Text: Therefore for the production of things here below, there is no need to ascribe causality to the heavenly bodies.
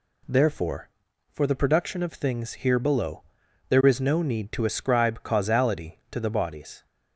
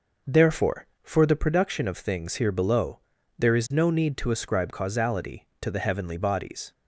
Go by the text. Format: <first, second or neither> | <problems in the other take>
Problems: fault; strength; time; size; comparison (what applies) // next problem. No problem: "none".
second | skips "heavenly"; at 6.2 s